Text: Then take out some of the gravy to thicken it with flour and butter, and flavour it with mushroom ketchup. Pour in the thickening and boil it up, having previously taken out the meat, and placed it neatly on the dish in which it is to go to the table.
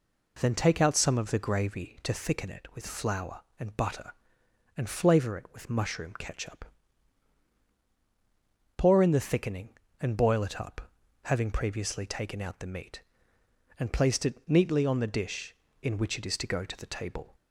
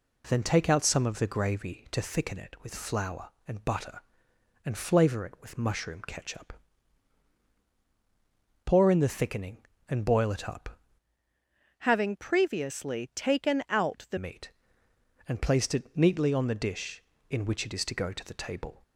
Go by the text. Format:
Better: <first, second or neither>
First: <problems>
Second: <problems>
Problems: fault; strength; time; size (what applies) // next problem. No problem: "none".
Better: first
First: none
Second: changes voice from "having" to "the"; from 11.7 to 14.1 s; 2.4 s long